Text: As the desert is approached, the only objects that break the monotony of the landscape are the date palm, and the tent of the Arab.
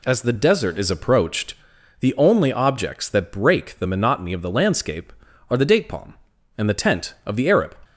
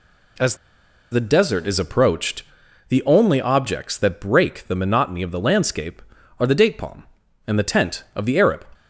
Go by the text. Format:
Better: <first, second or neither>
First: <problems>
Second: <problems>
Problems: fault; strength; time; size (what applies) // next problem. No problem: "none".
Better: first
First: none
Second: pauses between "As" and "the"; noticeable; at 0.5 s; 0.56 s long